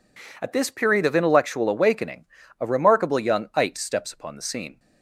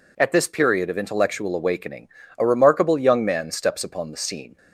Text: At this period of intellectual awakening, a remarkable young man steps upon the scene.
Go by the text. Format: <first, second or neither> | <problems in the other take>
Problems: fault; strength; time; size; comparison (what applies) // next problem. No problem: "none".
second | says "ite" for "man"; at 3.5 s